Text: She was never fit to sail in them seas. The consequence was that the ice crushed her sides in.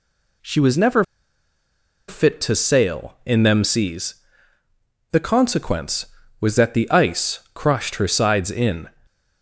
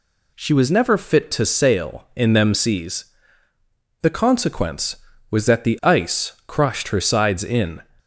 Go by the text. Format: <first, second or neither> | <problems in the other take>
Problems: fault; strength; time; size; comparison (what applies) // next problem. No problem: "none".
second | pauses between "never" and "fit"; at 1.0 s; 1.0 s long // stays silent after the last word; slight; from 8.8 s on; 0.6 s long